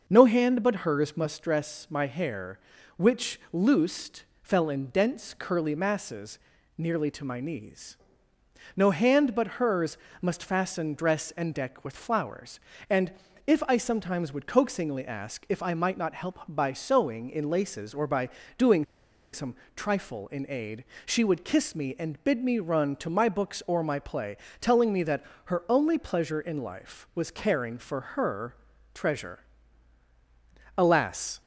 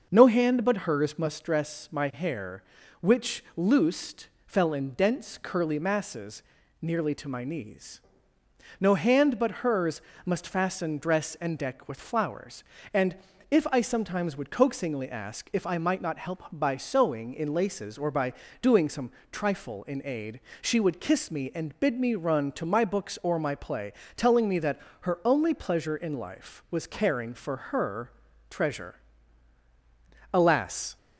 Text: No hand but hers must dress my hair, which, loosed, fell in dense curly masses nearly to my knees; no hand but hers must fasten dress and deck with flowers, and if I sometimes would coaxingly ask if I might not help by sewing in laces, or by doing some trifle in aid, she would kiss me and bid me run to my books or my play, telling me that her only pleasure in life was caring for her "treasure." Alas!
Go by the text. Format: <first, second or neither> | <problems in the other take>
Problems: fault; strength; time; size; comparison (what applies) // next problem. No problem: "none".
second | starts louder than the rest; noticeable; until 1.0 s; 6 dB; noticeable in the second // pauses between "masses" and "nearly"; at 6.3 s; 0.38 s long; also in the second // pauses between "hers" and "must"; slight; at 9.9 s; 0.24 s long; slight in the second // pauses between "and" and "if"; slight; at 13.1 s; 0.34 s long; slight in the second // pauses between "by" and "doing"; slight; at 18.2 s; 0.28 s long; slight in the second // pauses between "doing" and "some"; noticeable; at 18.8 s; 0.48 s long // pauses between "some" and "trifle"; slight; at 19.5 s; 0.20 s long; slight in the second // pauses between "that" and "her"; slight; at 25.2 s; 0.22 s long; slight in the second // pauses between "her" and "treasure"; at 28.5 s; 0.38 s long; also in the second